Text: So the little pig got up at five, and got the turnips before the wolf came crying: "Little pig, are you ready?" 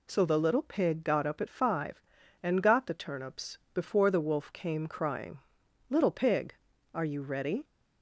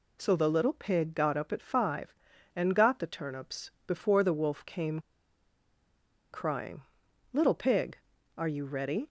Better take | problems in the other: first | pauses between "turnips" and "before"; slight; at 3.7 s; 0.16 s long; slight in the first // pauses between "came" and "crying"; strong; at 4.9 s; 1.3 s long

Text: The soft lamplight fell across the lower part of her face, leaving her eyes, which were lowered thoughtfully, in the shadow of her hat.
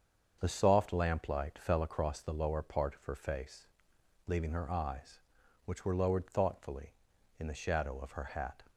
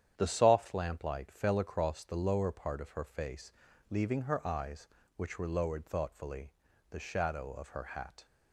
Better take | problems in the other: first | starts louder than the rest; strong; until 1.1 s; 9.5 dB; also in the first // skips "in"; at 6.7 s

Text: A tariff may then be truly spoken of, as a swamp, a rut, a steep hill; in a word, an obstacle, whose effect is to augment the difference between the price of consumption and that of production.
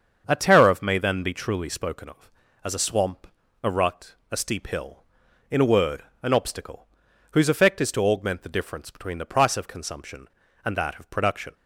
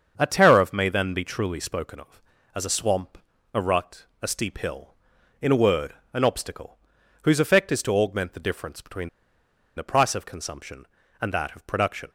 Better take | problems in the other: first | starts louder than the rest; until 1.1 s; 7 dB; also in the first // pauses between "between" and "the"; noticeable; at 9.0 s; 0.68 s long

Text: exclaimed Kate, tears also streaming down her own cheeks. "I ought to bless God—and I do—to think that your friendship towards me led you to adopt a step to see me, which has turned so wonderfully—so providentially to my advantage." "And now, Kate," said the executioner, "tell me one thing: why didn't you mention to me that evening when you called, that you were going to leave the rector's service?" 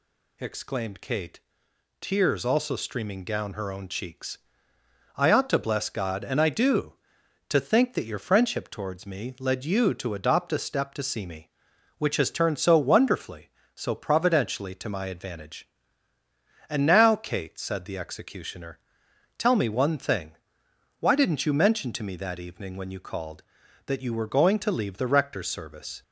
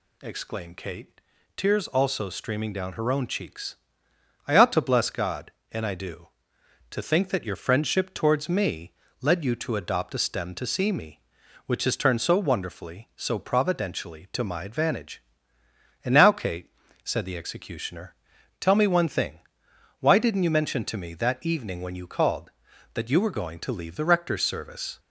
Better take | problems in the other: first | pauses between "me" and "led"; slight; at 8.9 s; 0.28 s long // says "stem" for "step"; at 10.1 s

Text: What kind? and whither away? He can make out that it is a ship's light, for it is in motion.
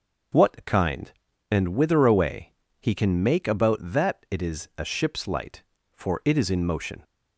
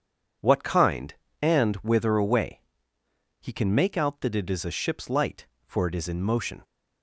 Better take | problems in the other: second | starts louder than the rest; until 1.7 s; 6 dB // says "about" for "out"; at 3.4 s

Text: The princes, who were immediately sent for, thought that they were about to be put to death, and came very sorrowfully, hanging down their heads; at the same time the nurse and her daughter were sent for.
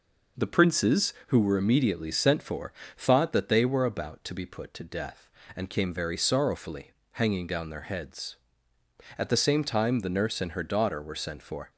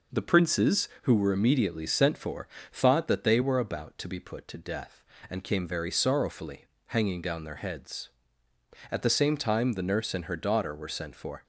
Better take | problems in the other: neither | none

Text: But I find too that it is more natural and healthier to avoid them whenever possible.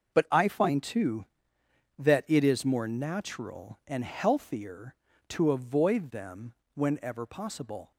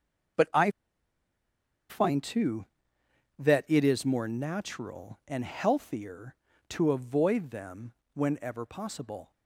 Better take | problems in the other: first | starts louder than the rest; until 2.6 s; 6 dB; also in the first // pauses between "I" and "find"; at 0.7 s; 1.1 s long // pauses between "them" and "whenever"; slight; at 7.9 s; 0.22 s long; slight in the first

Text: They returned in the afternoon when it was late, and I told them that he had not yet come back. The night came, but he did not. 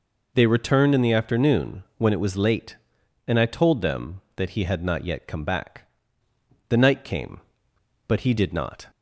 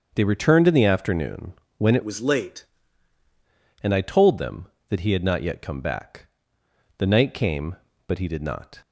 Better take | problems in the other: first | starts louder than the rest; until 1.1 s; 6.5 dB // pauses between "afternoon" and "when"; slight; at 1.5 s; 0.24 s long; slight in the first // changes voice from "was" to "late"; from 2.0 to 2.6 s; 0.6 s long

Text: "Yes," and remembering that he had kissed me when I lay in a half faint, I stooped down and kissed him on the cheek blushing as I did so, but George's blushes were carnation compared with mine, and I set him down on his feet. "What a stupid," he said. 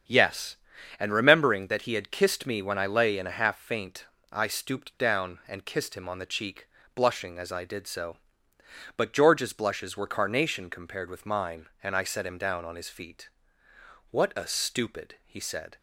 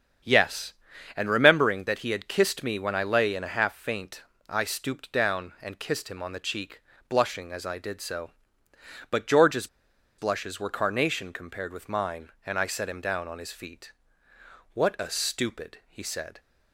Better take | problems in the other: first | starts louder than the rest; strong; until 1.6 s; 8 dB; strong in the first // pauses between "cheek" and "blushing"; slight; at 6.8 s; 0.28 s long; slight in the first // pauses between "George's" and "blushes"; noticeable; at 9.6 s; 0.52 s long

